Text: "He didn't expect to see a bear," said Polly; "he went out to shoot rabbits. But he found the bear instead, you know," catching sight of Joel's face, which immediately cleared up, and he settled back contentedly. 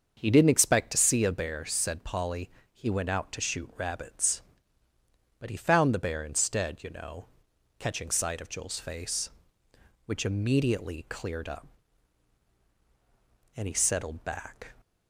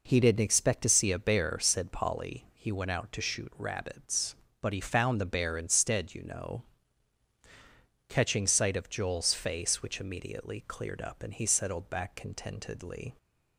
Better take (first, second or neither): second